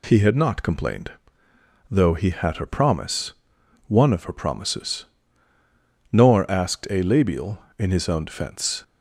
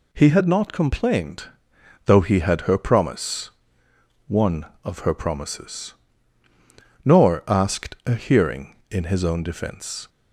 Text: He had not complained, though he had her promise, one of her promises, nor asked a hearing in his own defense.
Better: second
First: says "labial" for "hearing"; at 7.0 s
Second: none

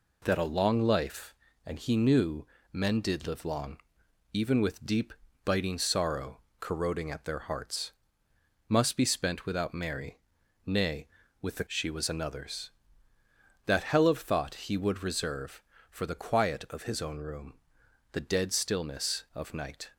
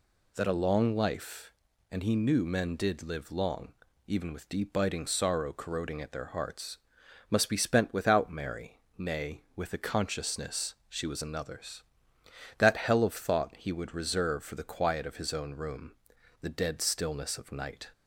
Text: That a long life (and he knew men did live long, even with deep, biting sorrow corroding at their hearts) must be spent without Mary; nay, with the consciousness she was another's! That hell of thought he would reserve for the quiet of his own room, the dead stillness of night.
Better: second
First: pauses between "knew" and "men"; slight; at 2.4 s; 0.24 s long // pauses between "sorrow" and "corroding"; slight; at 6.3 s; 0.22 s long // skips "consciousness"; at 11.6 s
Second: none

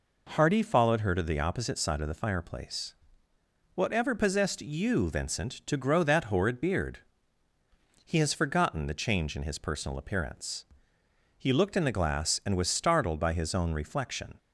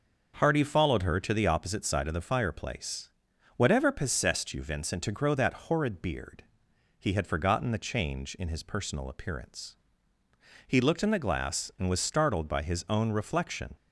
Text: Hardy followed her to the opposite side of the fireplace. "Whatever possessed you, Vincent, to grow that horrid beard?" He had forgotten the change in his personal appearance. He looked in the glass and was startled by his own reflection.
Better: second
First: says "has" for "had"; at 8.1 s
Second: none

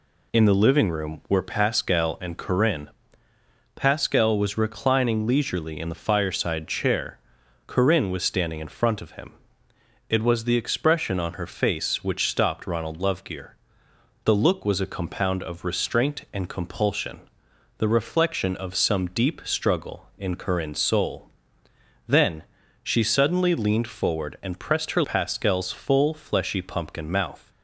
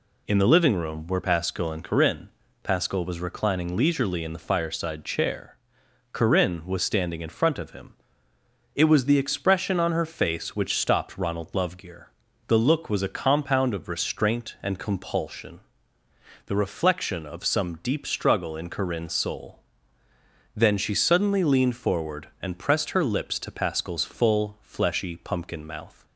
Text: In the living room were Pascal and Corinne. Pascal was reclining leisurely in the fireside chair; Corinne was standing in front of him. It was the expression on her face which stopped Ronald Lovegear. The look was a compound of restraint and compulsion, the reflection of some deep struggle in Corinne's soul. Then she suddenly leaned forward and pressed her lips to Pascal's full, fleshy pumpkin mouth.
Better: second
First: pauses between "Then" and "she"; at 22.4 s; 0.40 s long // skips "lips to"; at 25.0 s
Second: none

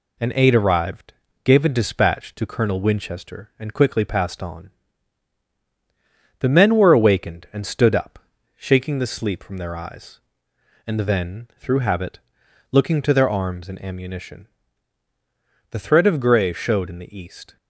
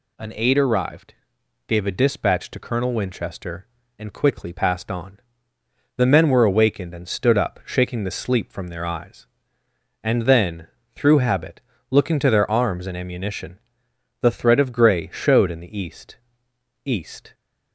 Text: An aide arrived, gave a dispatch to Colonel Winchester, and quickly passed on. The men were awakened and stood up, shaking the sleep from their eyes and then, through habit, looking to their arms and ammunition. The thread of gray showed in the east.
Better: first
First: none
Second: says "east" twice; at 16.8 s

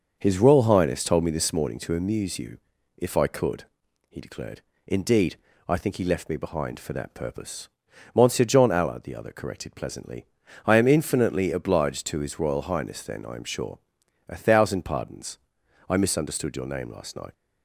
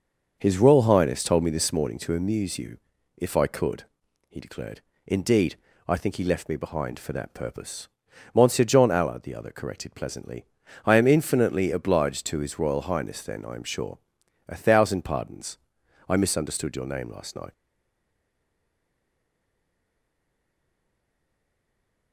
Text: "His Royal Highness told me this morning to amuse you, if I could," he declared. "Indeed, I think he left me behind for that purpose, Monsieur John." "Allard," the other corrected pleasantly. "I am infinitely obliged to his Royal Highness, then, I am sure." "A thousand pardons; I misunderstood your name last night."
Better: first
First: starts louder than the rest; noticeable; until 1.2 s; 6 dB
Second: starts louder than the rest; noticeable; until 1.4 s; 6 dB // stays silent after the last word; strong; from 17.5 s on; 4.6 s long

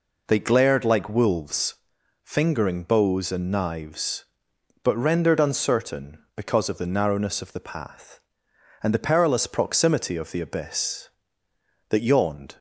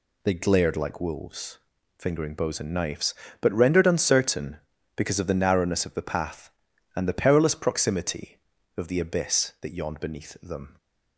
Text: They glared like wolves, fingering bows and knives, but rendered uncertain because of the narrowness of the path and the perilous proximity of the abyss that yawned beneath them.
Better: second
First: stops before "beneath them"; at 12.5 s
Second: none

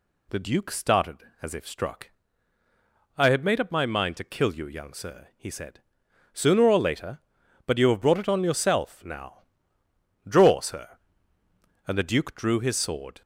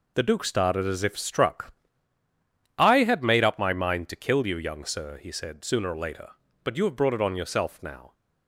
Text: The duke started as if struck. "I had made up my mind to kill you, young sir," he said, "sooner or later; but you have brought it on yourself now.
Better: second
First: goes on to say "Draw sir And the duke drew his sword"; strong; from 10.2 s on; 2.9 s long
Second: none

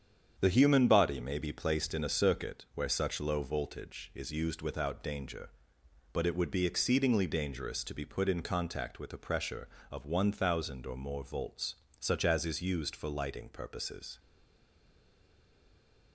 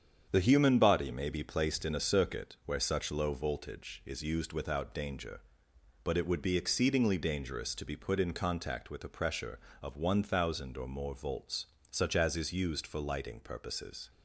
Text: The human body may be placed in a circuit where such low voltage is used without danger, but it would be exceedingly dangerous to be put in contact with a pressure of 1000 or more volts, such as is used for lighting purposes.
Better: second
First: starts louder than the rest; strong; until 1.3 s; 8 dB // stays silent after the last word; noticeable; from 14.1 s on; 2.0 s long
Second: starts louder than the rest; strong; until 1.3 s; 8 dB

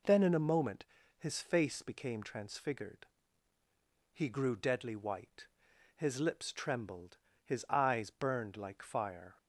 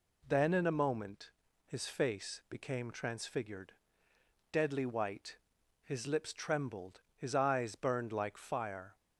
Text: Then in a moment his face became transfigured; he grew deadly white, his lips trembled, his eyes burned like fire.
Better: first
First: pauses between "moment" and "his"; slight; at 0.8 s; 0.34 s long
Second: pauses between "moment" and "his"; slight; at 1.3 s; 0.34 s long // skips "he grew"; at 4.1 s

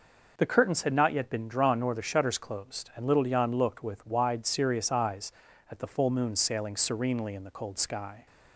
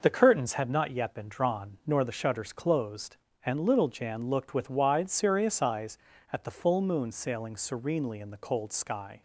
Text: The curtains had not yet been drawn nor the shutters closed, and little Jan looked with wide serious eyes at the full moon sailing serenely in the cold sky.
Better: neither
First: none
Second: none

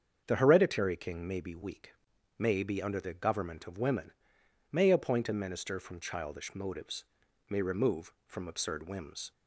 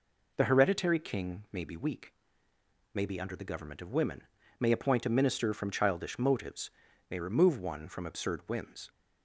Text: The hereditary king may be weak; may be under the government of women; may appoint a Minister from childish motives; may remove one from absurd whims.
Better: second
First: starts louder than the rest; strong; until 1.2 s; 7 dB // skips "one"; at 8.1 s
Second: none

